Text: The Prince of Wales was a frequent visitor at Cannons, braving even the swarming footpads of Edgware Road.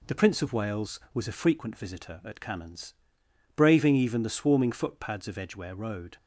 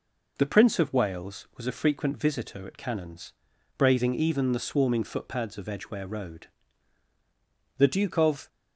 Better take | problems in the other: first | goes on to say "The Duke of"; noticeable; from 7.7 s on; 0.70 s long

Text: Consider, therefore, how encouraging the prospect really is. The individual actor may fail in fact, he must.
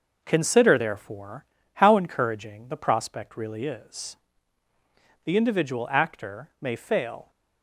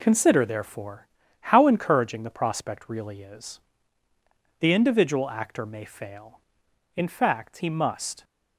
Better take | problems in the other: second | stops before "in fact he must"; at 7.2 s

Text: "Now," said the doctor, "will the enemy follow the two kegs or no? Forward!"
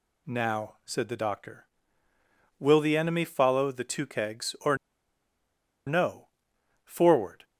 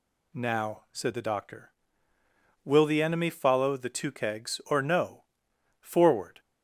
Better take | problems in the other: second | pauses between "or" and "no"; at 4.7 s; 1.1 s long

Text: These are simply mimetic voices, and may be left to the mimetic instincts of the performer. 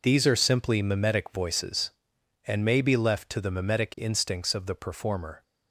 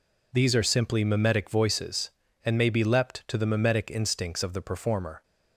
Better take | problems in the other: first | says "leapt" for "left"; at 2.8 s

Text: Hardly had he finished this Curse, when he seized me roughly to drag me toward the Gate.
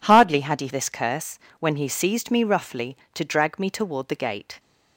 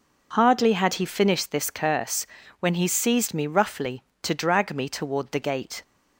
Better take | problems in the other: second | skips "finished"; at 0.6 s

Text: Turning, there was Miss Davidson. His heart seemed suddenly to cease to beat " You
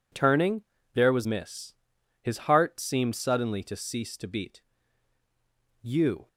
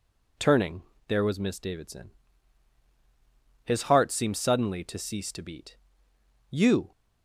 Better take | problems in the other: second | skips "Davidson"; at 1.9 s

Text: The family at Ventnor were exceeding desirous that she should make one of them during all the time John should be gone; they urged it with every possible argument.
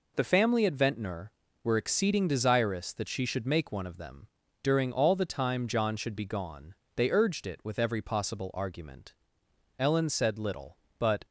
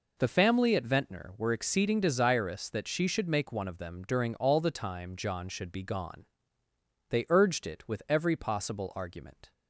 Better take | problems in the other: second | pauses between "them" and "during"; slight; at 4.2 s; 0.36 s long // goes on to say "Ellen said little but"; from 9.8 s on; 1.4 s long

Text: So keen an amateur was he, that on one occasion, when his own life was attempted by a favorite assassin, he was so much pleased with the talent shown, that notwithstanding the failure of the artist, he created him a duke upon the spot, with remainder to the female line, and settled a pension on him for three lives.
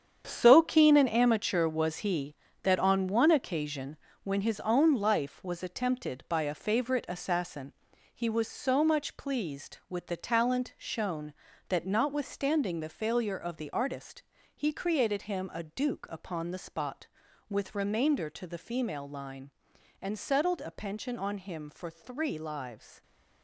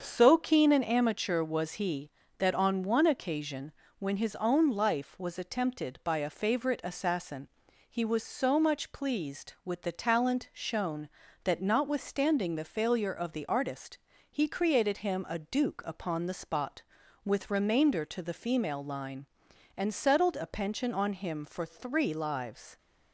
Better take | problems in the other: second | gets quieter; strong; throughout; 10 dB // starts louder than the rest; strong; until 1.2 s; 8 dB; also in the second

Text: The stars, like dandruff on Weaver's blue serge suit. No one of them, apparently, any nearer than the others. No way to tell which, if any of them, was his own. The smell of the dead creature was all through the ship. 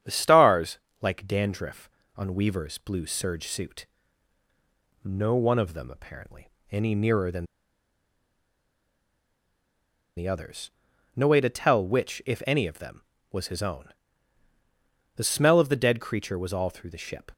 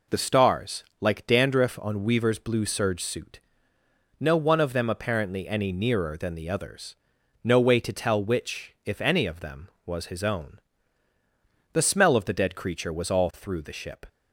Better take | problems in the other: second | starts louder than the rest; strong; until 1.2 s; 9 dB // pauses between "than" and "the"; strong; at 7.4 s; 2.7 s long

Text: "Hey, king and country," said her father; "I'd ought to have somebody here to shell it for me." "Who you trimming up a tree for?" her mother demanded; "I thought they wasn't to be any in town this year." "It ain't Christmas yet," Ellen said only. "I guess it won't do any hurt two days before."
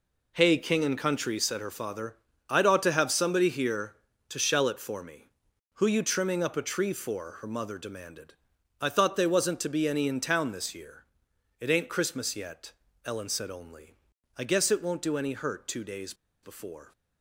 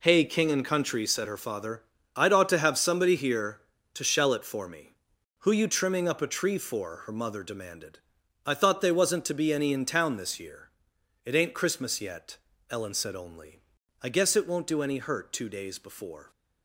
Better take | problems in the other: second | pauses between "days" and "before"; slight; at 16.1 s; 0.29 s long

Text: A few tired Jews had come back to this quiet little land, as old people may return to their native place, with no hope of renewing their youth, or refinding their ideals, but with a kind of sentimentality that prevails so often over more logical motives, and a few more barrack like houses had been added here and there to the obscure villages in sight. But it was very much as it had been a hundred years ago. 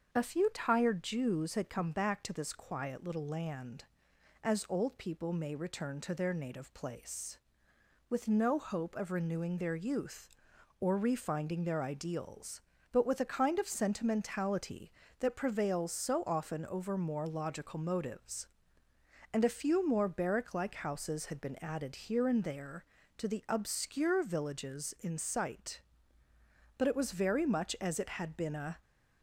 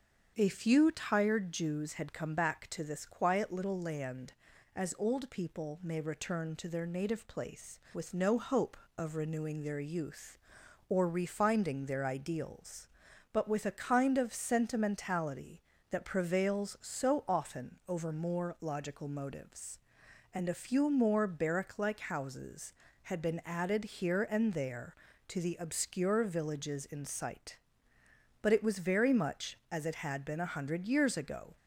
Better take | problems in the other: second | starts louder than the rest; until 1.1 s; 7 dB; strong in the second // stops before "hundred years ago"; at 28.8 s

